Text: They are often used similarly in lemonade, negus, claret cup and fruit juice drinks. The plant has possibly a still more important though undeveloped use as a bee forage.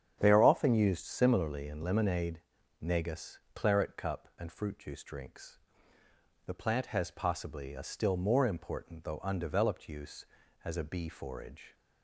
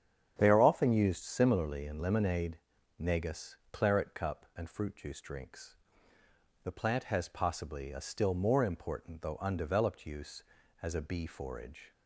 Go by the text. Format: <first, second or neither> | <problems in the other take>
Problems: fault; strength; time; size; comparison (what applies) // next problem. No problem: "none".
neither | starts louder than the rest; strong; the same in both